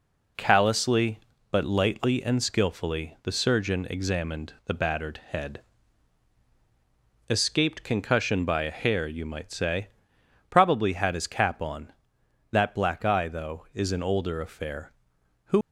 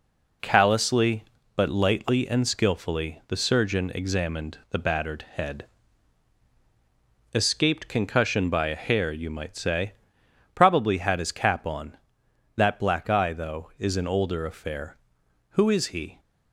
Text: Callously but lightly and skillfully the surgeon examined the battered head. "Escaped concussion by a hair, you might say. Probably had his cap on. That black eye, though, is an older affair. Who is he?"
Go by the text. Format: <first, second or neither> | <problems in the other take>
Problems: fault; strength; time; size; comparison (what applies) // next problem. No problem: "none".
second | stops before "is he"; at 15.6 s